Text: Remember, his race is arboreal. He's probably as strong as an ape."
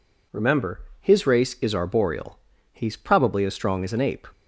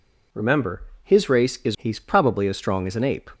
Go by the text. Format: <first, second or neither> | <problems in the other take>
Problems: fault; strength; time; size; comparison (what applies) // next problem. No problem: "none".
first | skips "arboreal"; at 1.7 s